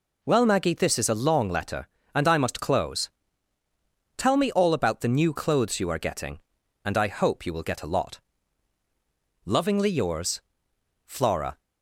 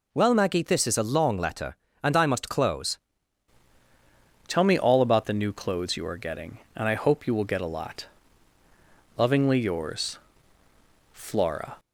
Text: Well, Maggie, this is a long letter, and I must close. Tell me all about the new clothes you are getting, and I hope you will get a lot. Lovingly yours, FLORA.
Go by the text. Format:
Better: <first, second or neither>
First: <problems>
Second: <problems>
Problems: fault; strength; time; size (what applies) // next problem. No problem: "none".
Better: first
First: none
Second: changes voice at "Tell"; from 4.4 s on; 7.3 s long